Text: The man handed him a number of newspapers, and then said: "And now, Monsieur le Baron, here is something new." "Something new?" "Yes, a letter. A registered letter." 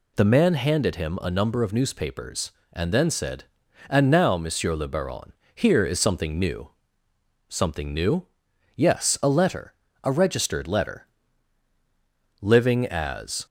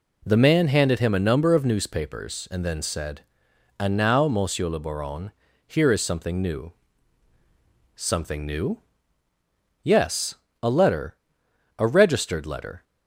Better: second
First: goes on to say "Living as"; noticeable; from 12.4 s on; 1.0 s long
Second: none

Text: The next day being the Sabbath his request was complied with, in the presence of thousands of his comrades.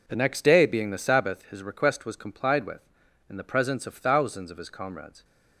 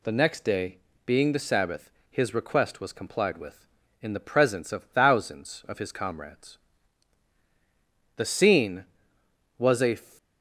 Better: first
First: none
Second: pauses between "day" and "being"; slight; at 0.7 s; 0.26 s long // pauses between "Sabbath" and "his"; slight; at 1.8 s; 0.22 s long // goes on to say "The scene was a"; strong; from 8.1 s on; 1.8 s long

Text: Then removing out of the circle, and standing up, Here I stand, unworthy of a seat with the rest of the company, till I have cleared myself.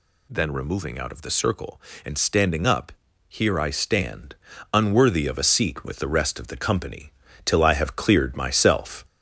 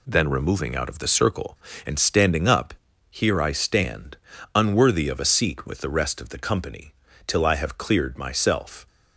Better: second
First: gets louder; throughout; 3.5 dB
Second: none

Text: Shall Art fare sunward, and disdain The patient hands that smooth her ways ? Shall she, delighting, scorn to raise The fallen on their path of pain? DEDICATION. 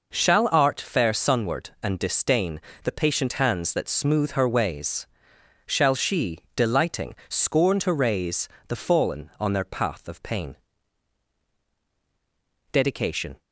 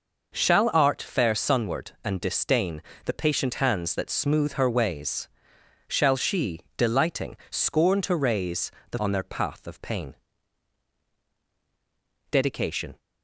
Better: first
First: pauses between "disdain" and "The"; slight; at 2.5 s; 0.24 s long // pauses between "raise" and "The"; slight; at 8.4 s; 0.18 s long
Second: pauses between "disdain" and "The"; slight; at 2.8 s; 0.24 s long // pauses between "raise" and "The"; slight; at 8.7 s; 0.18 s long // skips "fallen"; at 8.9 s

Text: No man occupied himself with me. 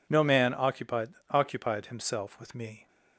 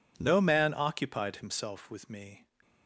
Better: second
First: says "occupied" twice; at 1.3 s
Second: none

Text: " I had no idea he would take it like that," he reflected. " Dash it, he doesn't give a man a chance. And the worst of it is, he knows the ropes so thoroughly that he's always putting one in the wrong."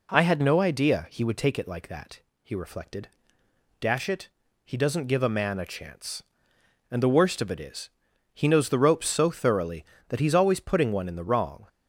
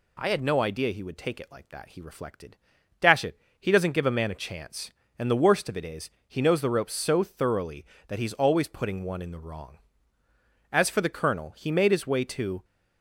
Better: first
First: none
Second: goes on to say "As for the Colonel he made his way to"; strong; from 10.7 s on; 1.9 s long

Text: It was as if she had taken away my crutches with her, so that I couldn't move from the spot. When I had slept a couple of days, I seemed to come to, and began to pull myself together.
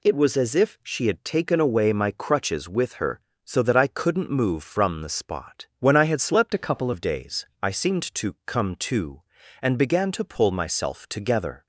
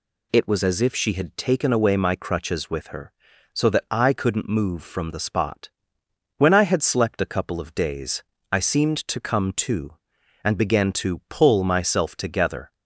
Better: second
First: changes voice from "a" to "couple"; from 6.5 to 6.9 s; 0.4 s long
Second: none

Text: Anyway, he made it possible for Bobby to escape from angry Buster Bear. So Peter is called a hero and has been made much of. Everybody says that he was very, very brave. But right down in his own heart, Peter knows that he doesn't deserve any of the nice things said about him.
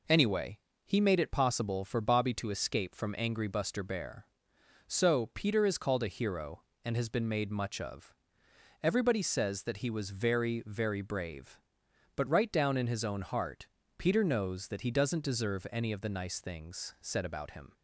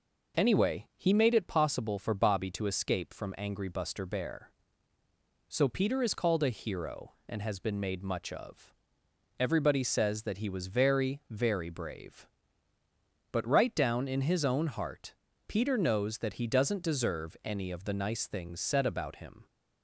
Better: neither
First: none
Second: none

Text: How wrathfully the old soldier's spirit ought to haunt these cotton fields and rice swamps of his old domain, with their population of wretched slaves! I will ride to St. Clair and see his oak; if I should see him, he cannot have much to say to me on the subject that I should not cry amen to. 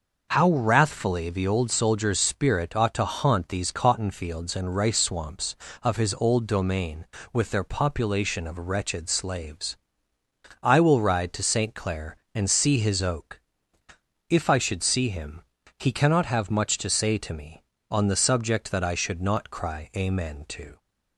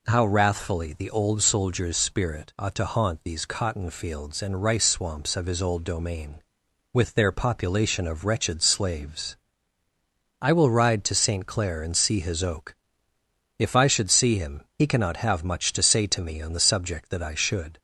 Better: first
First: none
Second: stops before "not cry amen to"; at 17.7 s

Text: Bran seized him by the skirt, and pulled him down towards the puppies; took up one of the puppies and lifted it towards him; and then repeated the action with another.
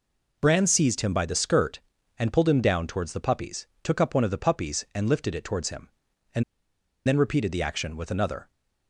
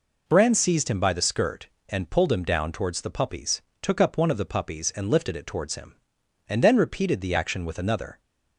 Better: second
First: pauses between "and" and "then"; noticeable; at 6.4 s; 0.64 s long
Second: none

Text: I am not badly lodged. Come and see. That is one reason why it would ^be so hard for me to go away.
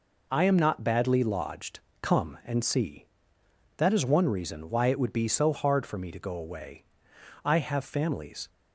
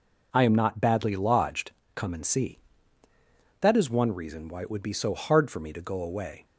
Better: second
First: goes on to say "I have families"; noticeable; from 7.4 s on; 1.0 s long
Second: none

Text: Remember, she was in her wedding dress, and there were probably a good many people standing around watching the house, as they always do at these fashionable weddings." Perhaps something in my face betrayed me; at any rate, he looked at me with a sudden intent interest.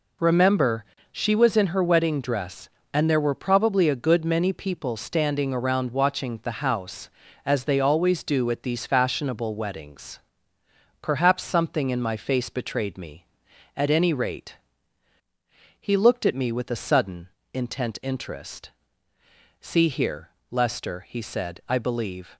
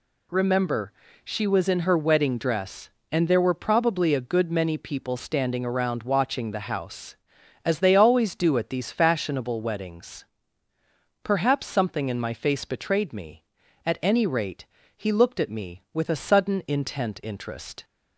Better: second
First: pauses between "sudden" and "intent"; slight; at 17.2 s; 0.24 s long // goes on to say "See here Lester he said I believe"; strong; from 19.6 s on; 2.7 s long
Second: none

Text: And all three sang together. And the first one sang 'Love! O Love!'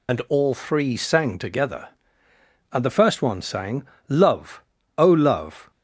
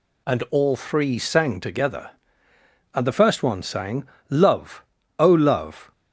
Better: second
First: loses the start of "And"; at 0.0 s; 50 ms // pauses between "sang" and "Love"; slight; at 3.8 s; 0.22 s long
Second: pauses between "sang" and "Love"; slight; at 4.0 s; 0.22 s long

